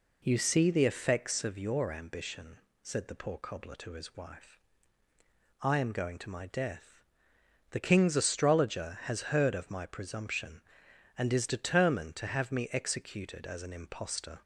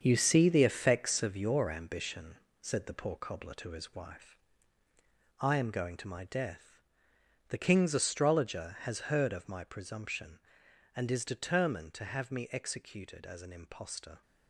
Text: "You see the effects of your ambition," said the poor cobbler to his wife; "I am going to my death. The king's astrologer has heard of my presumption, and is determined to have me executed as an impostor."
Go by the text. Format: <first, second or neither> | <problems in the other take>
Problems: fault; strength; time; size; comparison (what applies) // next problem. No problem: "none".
first | gets quieter; strong; throughout; 8.5 dB